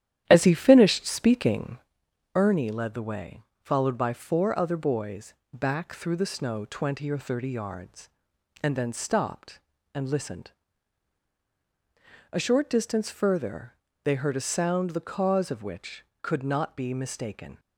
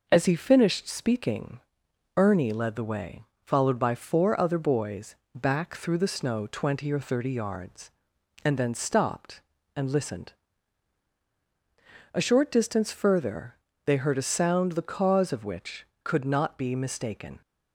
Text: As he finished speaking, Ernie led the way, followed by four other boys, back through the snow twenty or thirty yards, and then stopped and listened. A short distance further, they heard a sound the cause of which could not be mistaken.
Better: second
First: starts louder than the rest; strong; until 2.0 s; 11 dB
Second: none

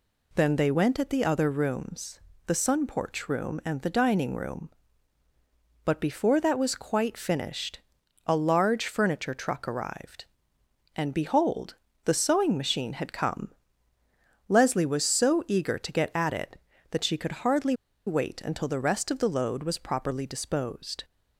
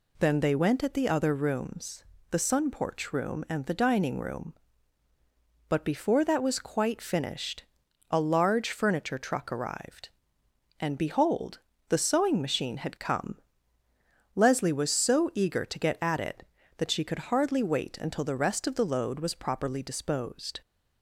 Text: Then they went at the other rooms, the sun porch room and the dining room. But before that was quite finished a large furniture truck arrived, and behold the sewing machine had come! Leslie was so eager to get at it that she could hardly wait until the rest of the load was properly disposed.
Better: second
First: pauses between "finished" and "a"; at 7.8 s; 0.44 s long // pauses between "behold" and "the"; slight; at 11.7 s; 0.30 s long // pauses between "hardly" and "wait"; slight; at 17.7 s; 0.32 s long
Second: pauses between "finished" and "a"; at 7.6 s; 0.44 s long // pauses between "behold" and "the"; slight; at 11.5 s; 0.30 s long

